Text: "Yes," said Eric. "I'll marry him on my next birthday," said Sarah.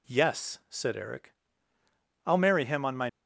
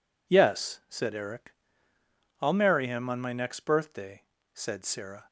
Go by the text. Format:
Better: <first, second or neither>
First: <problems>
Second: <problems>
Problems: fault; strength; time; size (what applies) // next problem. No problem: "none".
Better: second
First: stops before "next birthday said Sarah"; at 3.0 s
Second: none